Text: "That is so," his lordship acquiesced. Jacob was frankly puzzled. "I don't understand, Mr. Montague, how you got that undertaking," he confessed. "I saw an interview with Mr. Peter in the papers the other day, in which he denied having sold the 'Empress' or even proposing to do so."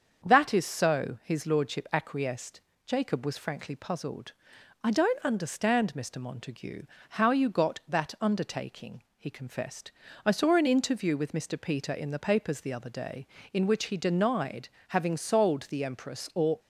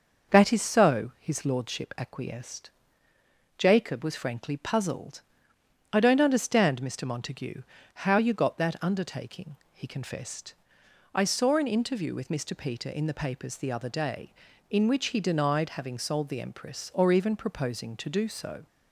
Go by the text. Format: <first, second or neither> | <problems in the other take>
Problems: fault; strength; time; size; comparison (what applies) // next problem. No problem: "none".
second | starts louder than the rest; until 1.3 s; 7 dB // pauses between "denied" and "having"; slight; at 14.6 s; 0.20 s long // stops before "even proposing to do so"; at 16.5 s